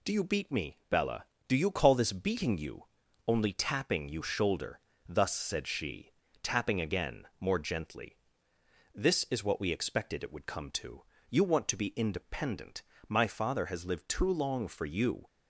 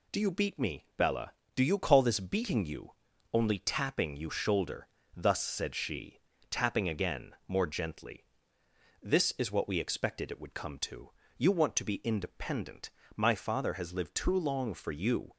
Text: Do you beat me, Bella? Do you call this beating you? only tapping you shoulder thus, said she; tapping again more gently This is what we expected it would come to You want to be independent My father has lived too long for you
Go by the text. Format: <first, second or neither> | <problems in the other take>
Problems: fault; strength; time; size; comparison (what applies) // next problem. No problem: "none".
neither | pauses between "shoulder" and "thus"; slight; the same in both // pauses between "again" and "more"; slight; the same in both // pauses between "gently" and "This"; noticeable; the same in both // pauses between "to" and "You"; slight; the same in both // pauses between "independent" and "My"; slight; the same in both